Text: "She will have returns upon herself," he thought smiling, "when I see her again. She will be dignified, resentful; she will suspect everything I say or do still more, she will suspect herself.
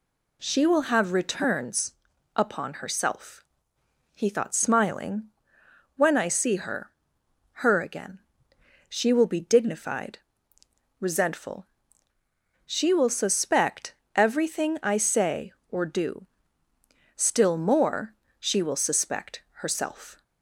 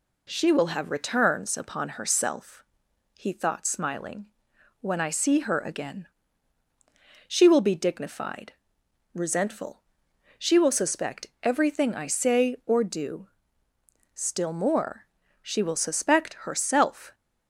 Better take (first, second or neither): second